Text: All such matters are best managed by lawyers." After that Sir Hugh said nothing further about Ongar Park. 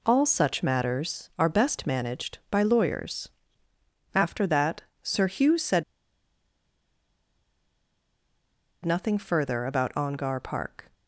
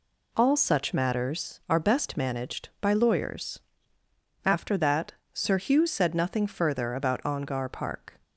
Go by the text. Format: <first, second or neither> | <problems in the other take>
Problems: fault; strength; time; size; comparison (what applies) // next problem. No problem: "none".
second | pauses between "that" and "Sir"; slight; at 4.8 s; 0.22 s long; slight in the second // pauses between "said" and "nothing"; strong; at 5.8 s; 3.0 s long